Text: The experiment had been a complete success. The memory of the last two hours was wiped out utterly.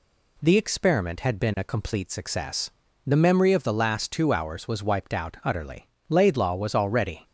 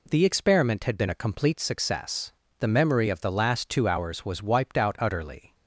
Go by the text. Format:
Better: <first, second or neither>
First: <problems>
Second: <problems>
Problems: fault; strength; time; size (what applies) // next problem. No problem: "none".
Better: second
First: goes on to say "Laidlaw was already"; noticeable; from 6.0 s on; 1.1 s long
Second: none